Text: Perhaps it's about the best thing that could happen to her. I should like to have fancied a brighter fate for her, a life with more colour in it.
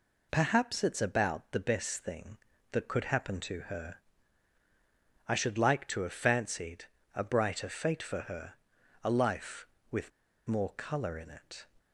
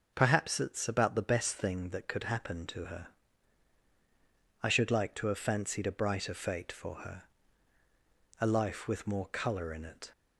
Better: second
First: pauses between "fancied" and "a"; slight; at 6.8 s; 0.32 s long // pauses between "with" and "more"; at 10.1 s; 0.38 s long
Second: none

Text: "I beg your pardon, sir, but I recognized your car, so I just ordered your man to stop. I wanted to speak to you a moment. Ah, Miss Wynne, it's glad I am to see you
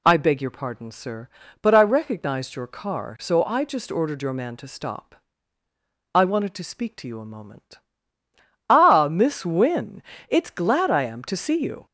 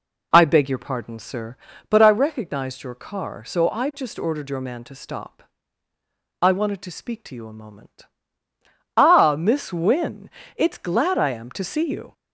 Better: first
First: none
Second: starts louder than the rest; until 2.1 s; 3.5 dB

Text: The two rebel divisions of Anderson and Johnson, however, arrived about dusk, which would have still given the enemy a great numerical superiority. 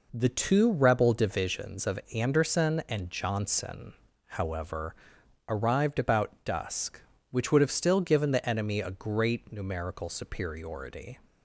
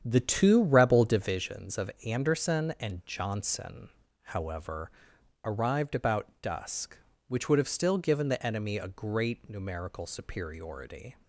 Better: first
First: pauses between "of" and "Anderson"; slight; at 1.9 s; 0.16 s long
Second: starts louder than the rest; strong; until 1.4 s; 8.5 dB // pauses between "of" and "Anderson"; slight; at 1.8 s; 0.16 s long

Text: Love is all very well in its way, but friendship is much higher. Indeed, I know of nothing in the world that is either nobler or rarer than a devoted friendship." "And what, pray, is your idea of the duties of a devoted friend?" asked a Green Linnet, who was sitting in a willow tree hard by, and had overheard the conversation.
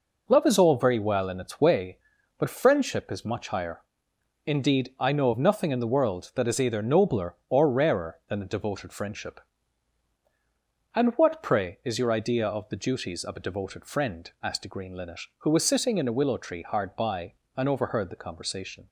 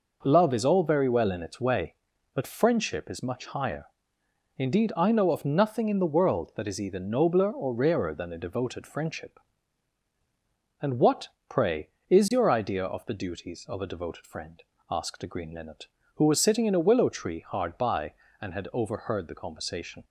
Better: second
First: skips "had"; at 17.6 s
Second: none

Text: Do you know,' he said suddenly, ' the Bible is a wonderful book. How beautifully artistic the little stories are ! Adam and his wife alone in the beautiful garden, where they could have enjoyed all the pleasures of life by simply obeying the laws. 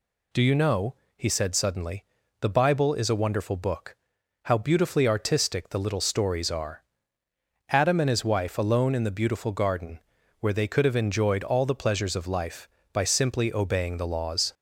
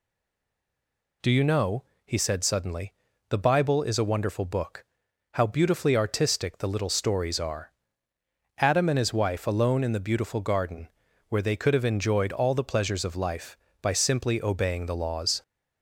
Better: first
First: none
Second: stays silent before the first word; noticeable; until 1.2 s; 1.2 s long

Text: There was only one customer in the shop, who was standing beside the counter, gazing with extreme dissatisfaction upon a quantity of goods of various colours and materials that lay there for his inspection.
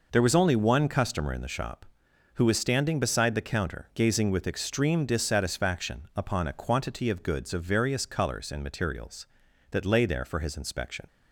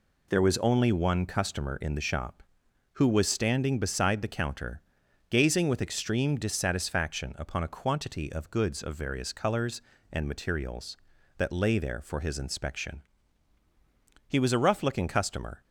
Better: first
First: none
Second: goes on to say "He was a rough looking customer"; from 14.2 s on; 1.3 s long

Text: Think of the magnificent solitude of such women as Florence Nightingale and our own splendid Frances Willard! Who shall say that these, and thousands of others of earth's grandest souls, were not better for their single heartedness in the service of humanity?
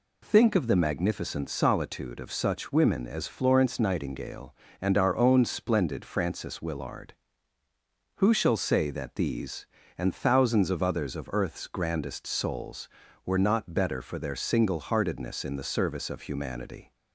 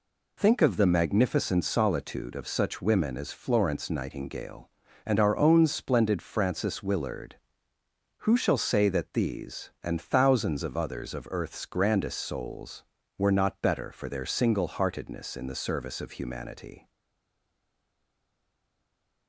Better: first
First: none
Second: stays silent after the last word; from 16.8 s on; 2.4 s long

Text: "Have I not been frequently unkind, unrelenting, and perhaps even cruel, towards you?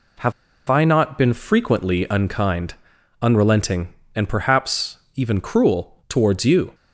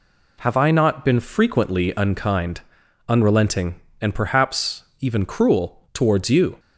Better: second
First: pauses between "Have" and "I"; slight; at 0.3 s; 0.35 s long // pauses between "perhaps" and "even"; slight; at 4.9 s; 0.18 s long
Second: pauses between "perhaps" and "even"; slight; at 4.8 s; 0.17 s long

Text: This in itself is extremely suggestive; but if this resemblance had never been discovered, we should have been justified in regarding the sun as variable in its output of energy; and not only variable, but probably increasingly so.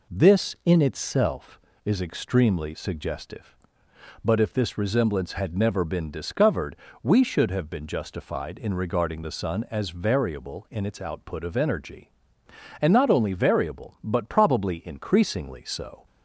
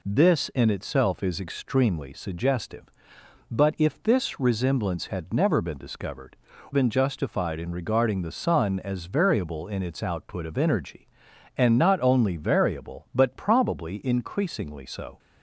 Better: first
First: none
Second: skips "we should have"; at 6.5 s

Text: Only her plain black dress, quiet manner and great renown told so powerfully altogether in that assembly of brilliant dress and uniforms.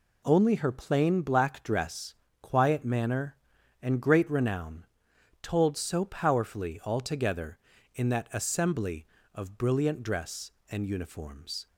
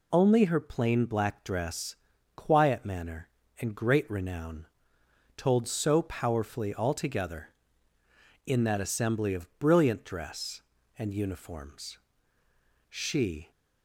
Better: first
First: pauses between "renown" and "told"; noticeable; at 4.8 s; 0.56 s long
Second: pauses between "renown" and "told"; noticeable; at 4.6 s; 0.70 s long // goes on to say "She"; noticeable; from 12.8 s on; 0.62 s long

